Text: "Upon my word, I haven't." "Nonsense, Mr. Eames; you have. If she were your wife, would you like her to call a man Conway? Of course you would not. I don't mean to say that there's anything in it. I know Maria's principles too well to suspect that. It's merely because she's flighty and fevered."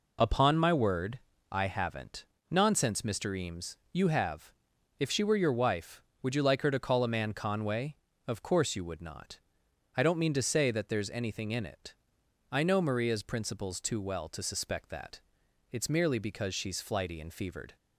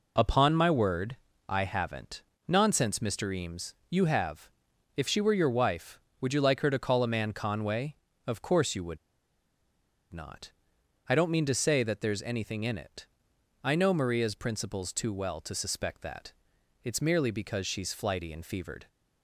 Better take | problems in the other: first | pauses between "would" and "not"; at 8.9 s; 1.1 s long

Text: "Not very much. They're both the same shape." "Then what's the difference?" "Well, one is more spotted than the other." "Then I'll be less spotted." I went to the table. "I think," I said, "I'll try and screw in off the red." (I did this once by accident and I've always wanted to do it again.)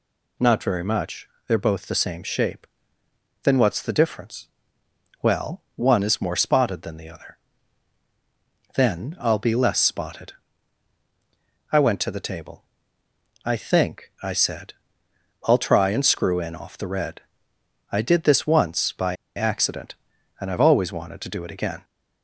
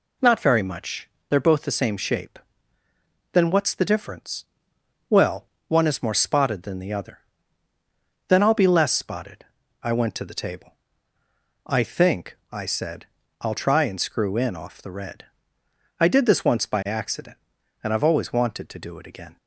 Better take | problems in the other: second | pauses between "by" and "accident"; slight; at 19.1 s; 0.20 s long

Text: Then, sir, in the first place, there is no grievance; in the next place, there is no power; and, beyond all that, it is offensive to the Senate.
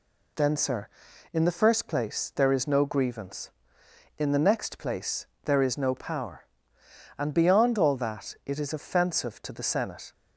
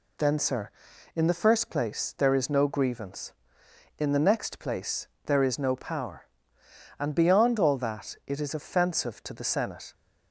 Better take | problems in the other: neither | none

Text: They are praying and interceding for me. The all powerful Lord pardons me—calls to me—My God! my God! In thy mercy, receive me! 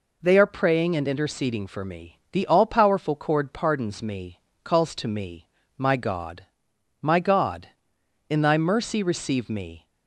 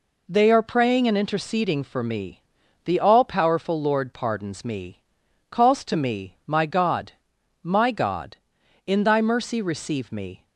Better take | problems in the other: second | says "Cord" for "Lord"; at 3.1 s

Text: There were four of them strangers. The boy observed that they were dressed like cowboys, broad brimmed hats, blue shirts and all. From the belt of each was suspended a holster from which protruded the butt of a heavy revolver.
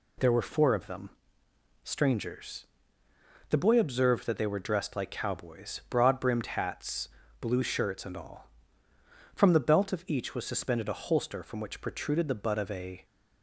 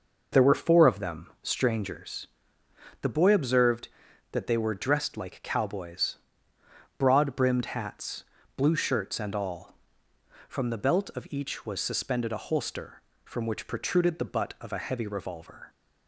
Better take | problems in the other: second | pauses between "them" and "strangers"; noticeable; at 1.1 s; 0.72 s long // stops before "heavy revolver"; at 13.0 s

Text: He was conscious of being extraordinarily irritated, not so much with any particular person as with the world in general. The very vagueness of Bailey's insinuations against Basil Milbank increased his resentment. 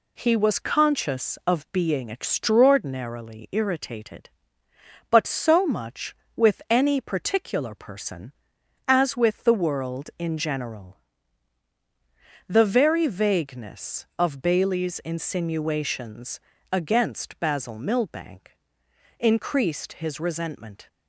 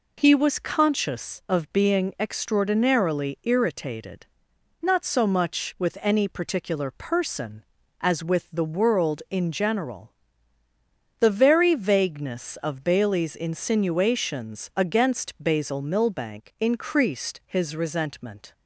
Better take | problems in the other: second | says "but" for "not"; at 5.1 s // pauses between "insinuations" and "against"; slight; at 16.3 s; 0.32 s long // pauses between "Milbank" and "increased"; noticeable; at 18.5 s; 0.64 s long

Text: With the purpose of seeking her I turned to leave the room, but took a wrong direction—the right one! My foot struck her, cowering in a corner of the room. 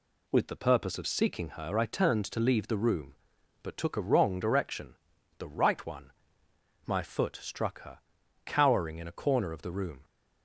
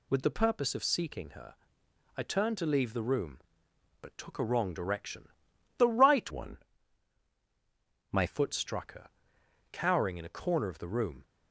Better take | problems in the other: first | pauses between "her" and "I"; noticeable; at 1.5 s; 0.62 s long // changes voice from "one" to "My"; from 6.2 to 8.2 s; 2.0 s long

